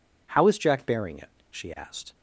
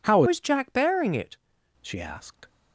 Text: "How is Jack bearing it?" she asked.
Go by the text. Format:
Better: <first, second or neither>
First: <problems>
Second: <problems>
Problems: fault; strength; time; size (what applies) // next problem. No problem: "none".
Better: first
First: none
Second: changes voice from "is" to "it"; from 0.2 to 1.3 s; 1.1 s long